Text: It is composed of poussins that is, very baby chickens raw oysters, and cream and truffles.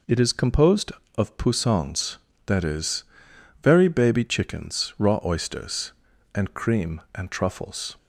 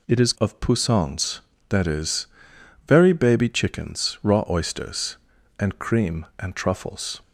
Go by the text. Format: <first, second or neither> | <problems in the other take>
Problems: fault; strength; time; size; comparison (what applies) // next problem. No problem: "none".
first | skips "composed"; at 0.3 s